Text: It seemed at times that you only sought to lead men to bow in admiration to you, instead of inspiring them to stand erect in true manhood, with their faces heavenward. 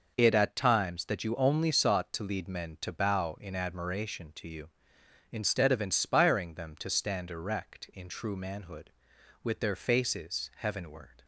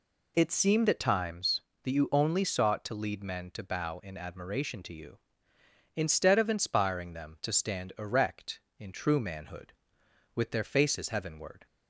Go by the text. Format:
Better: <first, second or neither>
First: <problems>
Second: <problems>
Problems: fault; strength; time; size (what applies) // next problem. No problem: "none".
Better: second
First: skips "seemed"; at 0.3 s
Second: none